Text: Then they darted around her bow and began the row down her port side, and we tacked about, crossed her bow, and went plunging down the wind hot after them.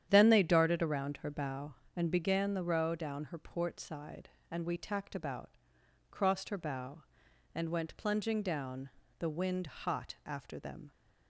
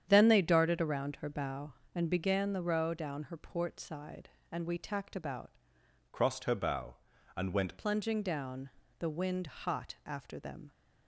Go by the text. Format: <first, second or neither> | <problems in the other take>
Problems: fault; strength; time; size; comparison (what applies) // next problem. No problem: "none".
first | starts louder than the rest; strong; until 1.1 s; 9 dB; strong in the first // changes voice from "crossed" to "went"; from 6.1 to 7.7 s; 1.6 s long // pauses between "down" and "the"; slight; at 8.7 s; 0.28 s long; slight in the first